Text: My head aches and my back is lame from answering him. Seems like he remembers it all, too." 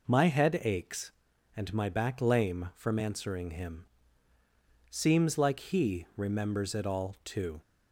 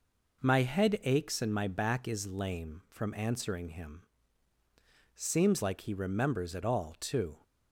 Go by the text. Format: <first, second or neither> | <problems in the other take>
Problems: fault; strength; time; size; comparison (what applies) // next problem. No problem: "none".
second | skips "is"; at 2.2 s